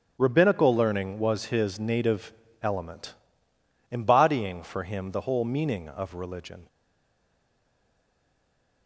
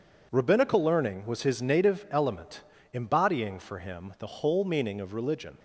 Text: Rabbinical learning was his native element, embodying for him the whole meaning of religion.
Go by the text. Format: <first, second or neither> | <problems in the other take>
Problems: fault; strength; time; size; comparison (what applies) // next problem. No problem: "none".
second | starts louder than the rest; strong; until 1.2 s; 10 dB // pauses between "native" and "element"; slight; at 2.3 s; 0.30 s long // stays silent after the last word; from 6.6 s on; 2.2 s long